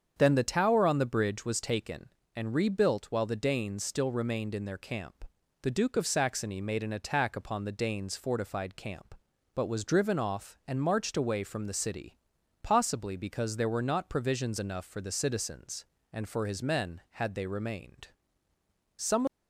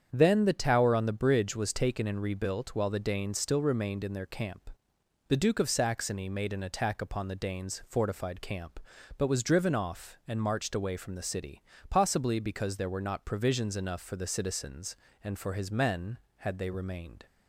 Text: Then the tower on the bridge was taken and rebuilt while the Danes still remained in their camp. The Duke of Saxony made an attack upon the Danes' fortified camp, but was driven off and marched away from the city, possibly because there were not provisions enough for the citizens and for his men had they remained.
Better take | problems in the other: second | starts louder than the rest; strong; until 1.1 s; 7.5 dB; strong in the second // goes on to say "Some of"; slight; from 18.9 s on; 0.32 s long

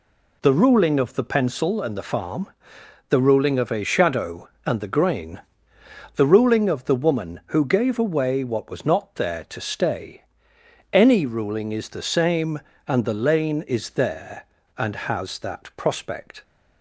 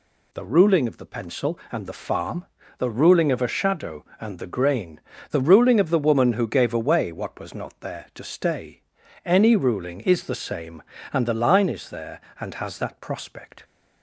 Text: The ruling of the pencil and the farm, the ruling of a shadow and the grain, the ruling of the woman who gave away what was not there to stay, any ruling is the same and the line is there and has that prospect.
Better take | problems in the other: second | says "lane" for "line"; at 13.1 s

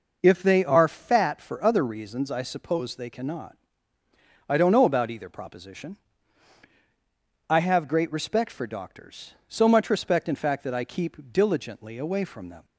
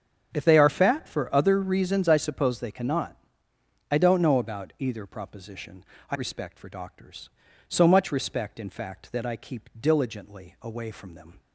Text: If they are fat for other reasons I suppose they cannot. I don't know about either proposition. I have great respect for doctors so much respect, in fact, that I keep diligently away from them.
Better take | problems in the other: first | starts louder than the rest; strong; until 1.3 s; 7.5 dB // skips "have great"; at 6.1 s

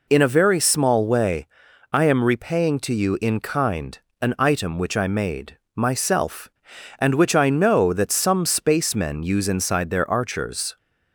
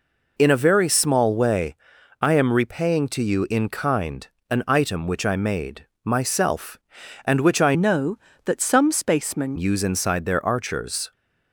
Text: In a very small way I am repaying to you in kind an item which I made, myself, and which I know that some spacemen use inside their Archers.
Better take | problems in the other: first | pauses between "way" and "I"; noticeable; at 1.7 s; 0.46 s long; noticeable in the first // pauses between "kind" and "an"; slight; at 4.2 s; 0.22 s long; slight in the first // changes voice from "know" to "spacemen"; from 7.7 to 9.5 s; 1.8 s long

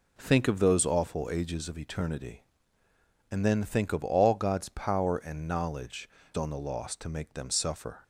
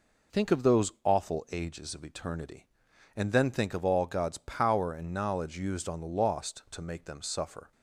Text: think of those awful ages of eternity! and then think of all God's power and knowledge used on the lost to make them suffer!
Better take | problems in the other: second | skips "used"; at 6.2 s

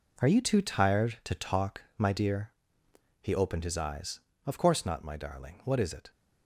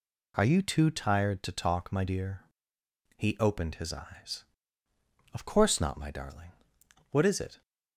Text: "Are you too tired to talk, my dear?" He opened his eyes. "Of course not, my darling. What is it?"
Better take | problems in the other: second | gets quieter; strong; throughout; 10 dB

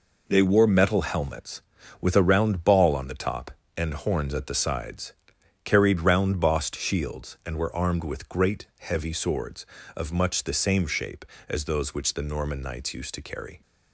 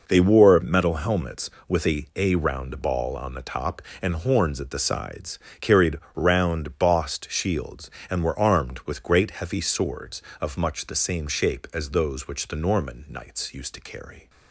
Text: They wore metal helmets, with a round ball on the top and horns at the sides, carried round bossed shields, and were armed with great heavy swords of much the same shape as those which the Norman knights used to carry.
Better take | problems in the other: first | says "a" twice; at 2.1 s // pauses between "carried" and "round"; slight; at 5.9 s; 0.16 s long

